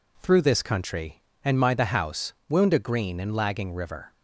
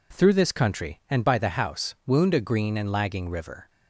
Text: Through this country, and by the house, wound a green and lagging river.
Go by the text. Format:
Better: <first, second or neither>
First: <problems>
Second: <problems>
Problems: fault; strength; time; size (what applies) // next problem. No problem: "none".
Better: second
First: says "my" for "by"; at 1.5 s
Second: none